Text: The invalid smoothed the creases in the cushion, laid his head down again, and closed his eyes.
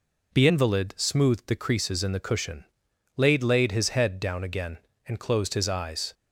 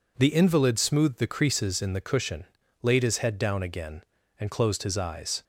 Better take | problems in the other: second | says "laid" twice; at 3.4 s

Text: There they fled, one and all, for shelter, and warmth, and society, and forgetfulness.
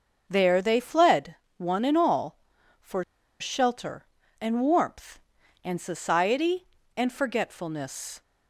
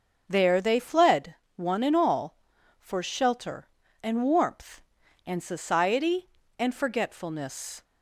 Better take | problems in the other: second | starts louder than the rest; noticeable; until 1.2 s; 6 dB; noticeable in the second // pauses between "for" and "shelter"; at 3.0 s; 0.37 s long

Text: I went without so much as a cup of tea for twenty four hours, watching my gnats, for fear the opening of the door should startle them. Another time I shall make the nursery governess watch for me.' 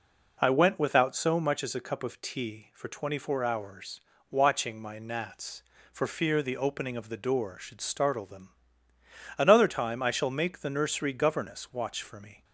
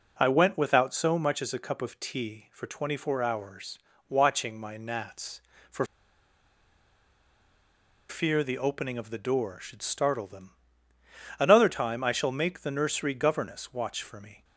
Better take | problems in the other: first | pauses between "for" and "fear"; strong; at 5.8 s; 2.2 s long

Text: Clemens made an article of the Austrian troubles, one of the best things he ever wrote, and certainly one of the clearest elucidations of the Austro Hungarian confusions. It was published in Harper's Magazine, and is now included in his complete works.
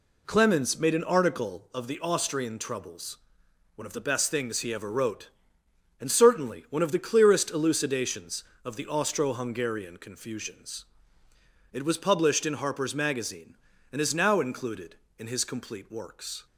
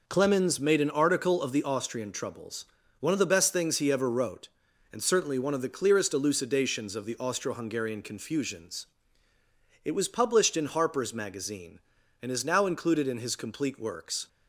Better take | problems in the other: neither | none

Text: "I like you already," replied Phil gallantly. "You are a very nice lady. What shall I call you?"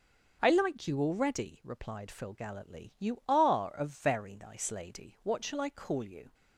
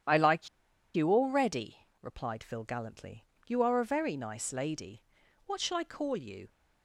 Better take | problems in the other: first | starts louder than the rest; strong; until 1.5 s; 9 dB; also in the first // pauses between "like" and "you"; noticeable; at 0.4 s; 0.46 s long

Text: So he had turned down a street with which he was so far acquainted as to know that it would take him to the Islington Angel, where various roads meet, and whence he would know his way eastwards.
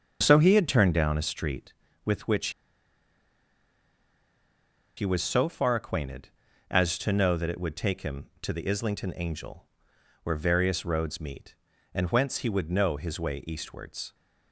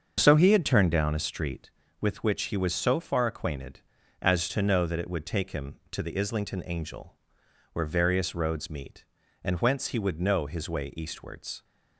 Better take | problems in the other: second | starts louder than the rest; until 1.2 s; 7 dB; also in the second // pauses between "which" and "he"; strong; at 2.4 s; 2.4 s long

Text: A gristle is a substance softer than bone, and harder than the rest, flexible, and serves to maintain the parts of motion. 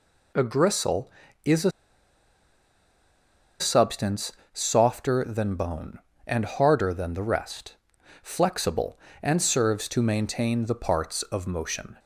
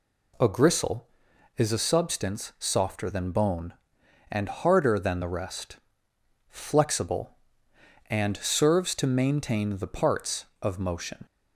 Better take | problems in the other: second | pauses between "a" and "substance"; strong; at 1.6 s; 1.9 s long // pauses between "substance" and "softer"; slight; at 4.3 s; 0.22 s long

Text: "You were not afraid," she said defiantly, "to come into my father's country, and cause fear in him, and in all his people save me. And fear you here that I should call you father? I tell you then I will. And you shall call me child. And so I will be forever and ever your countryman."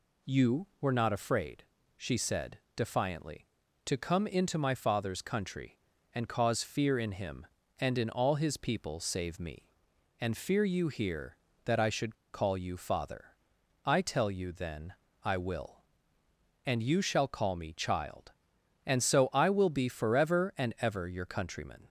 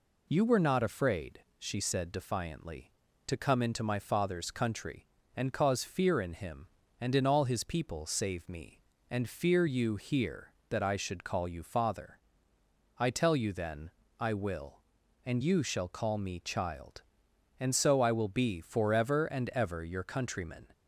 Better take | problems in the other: second | pauses between "said" and "defiantly"; slight; at 2.5 s; 0.18 s long // pauses between "should" and "call"; slight; at 12.1 s; 0.18 s long // pauses between "then" and "I"; slight; at 14.9 s; 0.30 s long; slight in the second

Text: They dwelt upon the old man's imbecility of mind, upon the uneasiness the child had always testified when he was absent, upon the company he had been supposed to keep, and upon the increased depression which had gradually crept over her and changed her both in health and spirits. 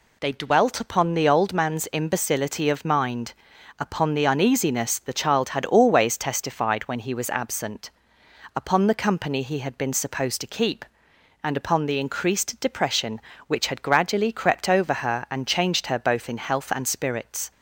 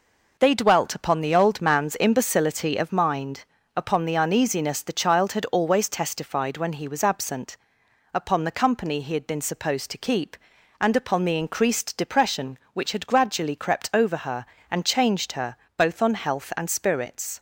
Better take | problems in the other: first | pauses between "her" and "both"; slight; at 15.5 s; 0.22 s long // says "on" for "in"; at 16.0 s

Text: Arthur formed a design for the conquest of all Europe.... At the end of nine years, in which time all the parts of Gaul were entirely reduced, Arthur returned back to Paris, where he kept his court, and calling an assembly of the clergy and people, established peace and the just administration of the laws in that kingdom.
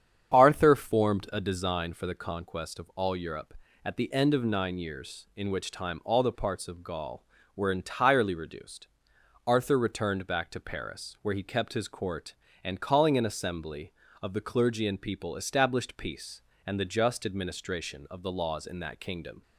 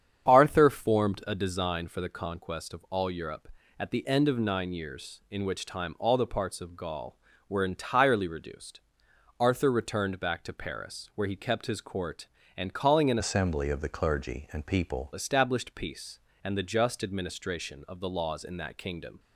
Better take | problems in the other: first | starts louder than the rest; strong; until 1.3 s; 8 dB; strong in the first // changes voice from "assembly" to "people"; from 13.1 to 15.0 s; 1.9 s long

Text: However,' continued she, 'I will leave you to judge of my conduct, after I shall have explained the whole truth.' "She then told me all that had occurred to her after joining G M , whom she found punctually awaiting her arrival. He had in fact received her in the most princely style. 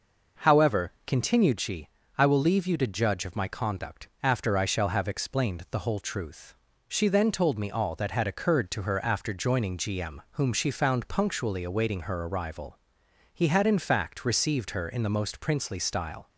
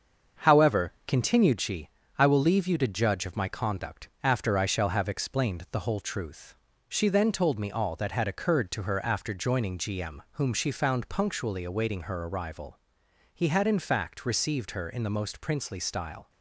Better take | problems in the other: first | gets quieter; noticeable; throughout; 5 dB

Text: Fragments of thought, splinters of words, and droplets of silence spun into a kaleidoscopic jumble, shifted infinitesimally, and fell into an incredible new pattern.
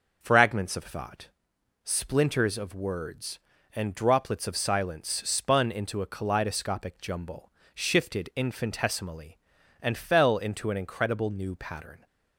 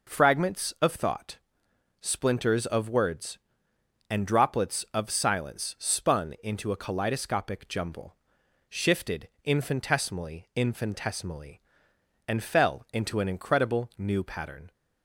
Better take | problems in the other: first | pauses between "shifted" and "infinitesimally"; slight; at 9.2 s; 0.16 s long // says "infinitesimally" twice; at 10.5 s

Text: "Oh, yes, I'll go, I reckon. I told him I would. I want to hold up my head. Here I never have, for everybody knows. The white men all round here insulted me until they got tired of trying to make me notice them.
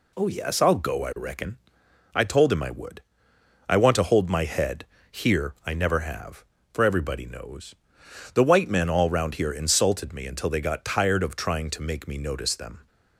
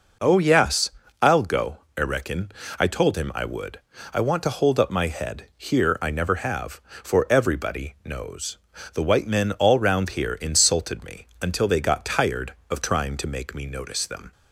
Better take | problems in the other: second | skips "up"; at 4.2 s

